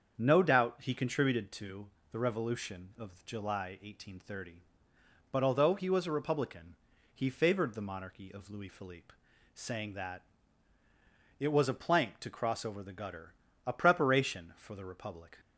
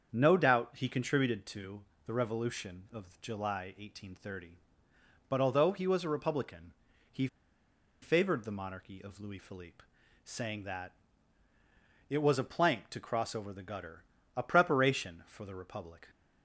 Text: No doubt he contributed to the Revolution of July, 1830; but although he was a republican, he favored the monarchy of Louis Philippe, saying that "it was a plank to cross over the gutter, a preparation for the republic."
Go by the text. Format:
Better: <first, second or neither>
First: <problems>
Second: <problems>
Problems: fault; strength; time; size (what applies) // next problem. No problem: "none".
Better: first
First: starts louder than the rest; strong; until 1.2 s; 7.5 dB // pauses between "to" and "the"; slight; at 1.8 s; 0.24 s long // pauses between "that" and "it"; at 10.2 s; 1.1 s long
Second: starts louder than the rest; strong; until 1.1 s; 7.5 dB // pauses between "to" and "the"; slight; at 1.8 s; 0.24 s long // pauses between "he" and "favored"; noticeable; at 7.2 s; 0.74 s long // pauses between "that" and "it"; at 10.9 s; 1.1 s long